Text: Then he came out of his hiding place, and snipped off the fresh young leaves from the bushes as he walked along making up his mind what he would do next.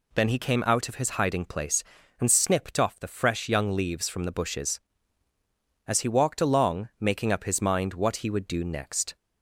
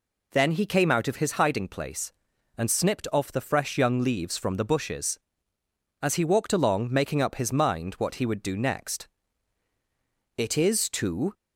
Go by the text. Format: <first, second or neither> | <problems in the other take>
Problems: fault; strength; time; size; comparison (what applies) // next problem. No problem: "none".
first | goes on to say "It is too"; noticeable; from 10.3 s on; 0.96 s long